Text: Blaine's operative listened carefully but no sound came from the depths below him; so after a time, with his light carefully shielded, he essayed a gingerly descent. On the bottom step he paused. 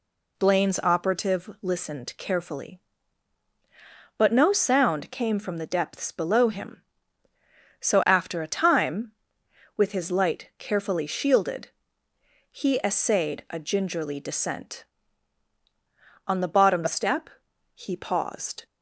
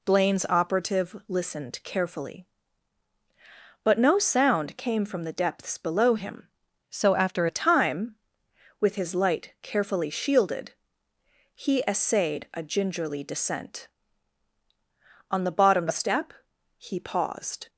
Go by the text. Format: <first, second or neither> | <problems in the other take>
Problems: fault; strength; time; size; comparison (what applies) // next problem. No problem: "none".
first | changes voice from "so" to "after"; from 6.8 to 7.4 s; 0.6 s long // pauses between "step" and "he"; noticeable; at 16.3 s; 0.46 s long; noticeable in the first